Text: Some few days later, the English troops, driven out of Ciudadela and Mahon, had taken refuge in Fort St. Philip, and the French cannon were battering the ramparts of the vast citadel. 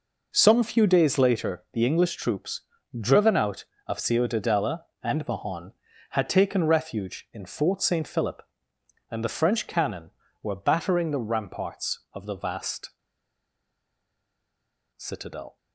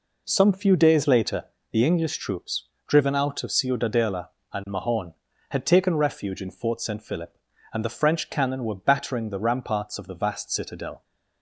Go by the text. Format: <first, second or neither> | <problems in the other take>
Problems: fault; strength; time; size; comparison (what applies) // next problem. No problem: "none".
second | pauses between "vast" and "citadel"; strong; at 12.8 s; 2.0 s long